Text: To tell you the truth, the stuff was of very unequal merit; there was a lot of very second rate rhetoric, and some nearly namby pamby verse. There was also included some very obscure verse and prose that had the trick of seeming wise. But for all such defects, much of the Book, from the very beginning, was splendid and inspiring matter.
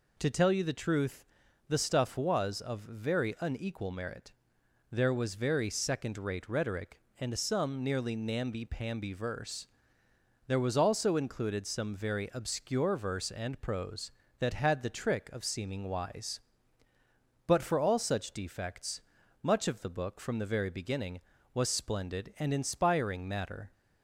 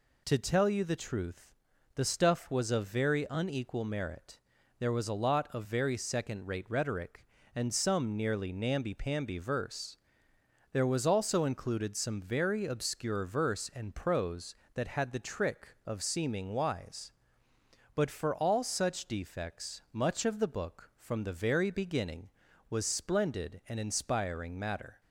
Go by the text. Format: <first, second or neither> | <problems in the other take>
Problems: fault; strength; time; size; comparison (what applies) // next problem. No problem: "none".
second | skips "a lot of"; at 5.3 s